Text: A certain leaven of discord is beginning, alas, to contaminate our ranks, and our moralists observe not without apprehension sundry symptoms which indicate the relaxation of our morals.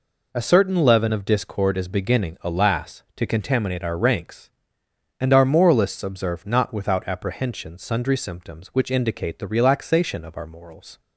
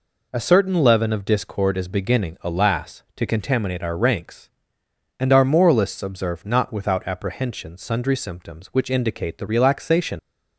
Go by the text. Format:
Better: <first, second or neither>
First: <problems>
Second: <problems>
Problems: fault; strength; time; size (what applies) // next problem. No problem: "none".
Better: first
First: none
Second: stops before "of our morals"; at 10.1 s